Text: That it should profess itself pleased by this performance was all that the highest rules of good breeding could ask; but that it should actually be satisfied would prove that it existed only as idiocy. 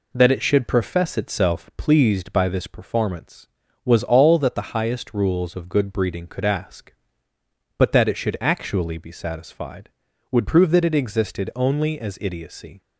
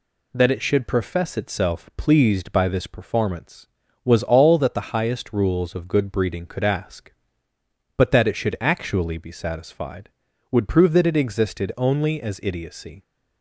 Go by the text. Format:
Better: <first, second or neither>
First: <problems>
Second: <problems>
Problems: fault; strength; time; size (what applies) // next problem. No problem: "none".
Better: second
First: starts louder than the rest; slight; until 1.7 s; 3 dB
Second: none